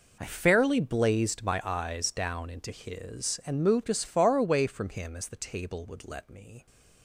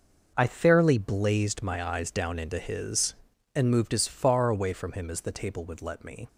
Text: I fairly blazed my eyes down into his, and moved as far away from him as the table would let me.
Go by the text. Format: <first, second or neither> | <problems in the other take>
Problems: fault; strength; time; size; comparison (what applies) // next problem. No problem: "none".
neither | none